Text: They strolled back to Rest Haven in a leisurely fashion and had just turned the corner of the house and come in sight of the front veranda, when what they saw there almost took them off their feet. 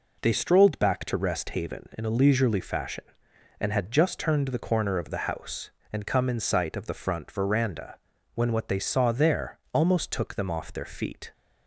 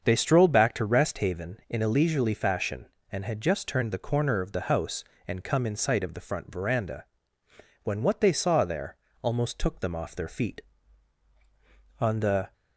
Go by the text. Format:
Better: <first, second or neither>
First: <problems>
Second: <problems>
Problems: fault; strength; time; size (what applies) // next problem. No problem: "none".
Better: first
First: none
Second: starts louder than the rest; until 1.0 s; 7 dB // pauses between "there" and "almost"; slight; at 8.9 s; 0.26 s long // goes on to say "On the"; from 12.0 s on; 0.52 s long